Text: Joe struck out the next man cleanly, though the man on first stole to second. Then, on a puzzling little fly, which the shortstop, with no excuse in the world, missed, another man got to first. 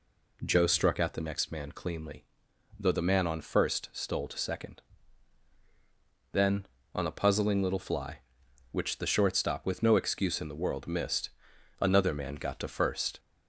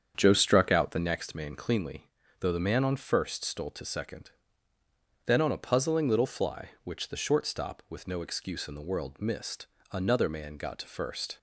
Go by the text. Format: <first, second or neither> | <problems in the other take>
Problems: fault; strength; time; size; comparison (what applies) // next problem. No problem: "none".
first | starts louder than the rest; strong; until 1.3 s; 7.5 dB